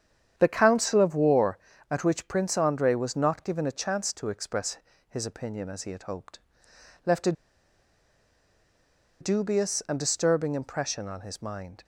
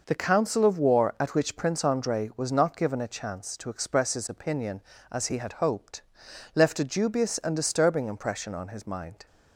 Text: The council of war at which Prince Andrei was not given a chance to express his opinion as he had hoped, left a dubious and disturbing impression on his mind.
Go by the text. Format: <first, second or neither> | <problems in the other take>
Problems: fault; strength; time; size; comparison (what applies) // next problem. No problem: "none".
second | starts louder than the rest; strong; until 1.3 s; 8.5 dB // pauses between "express" and "his"; slight; at 4.7 s; 0.32 s long // pauses between "a" and "dubious"; strong; at 7.3 s; 1.8 s long